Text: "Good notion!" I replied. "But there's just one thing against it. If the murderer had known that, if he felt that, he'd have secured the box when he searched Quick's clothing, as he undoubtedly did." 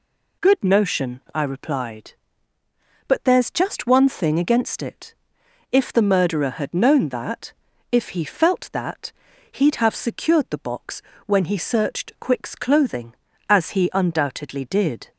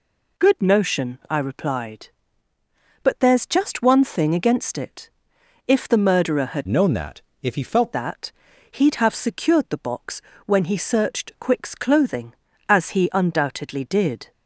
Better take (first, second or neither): first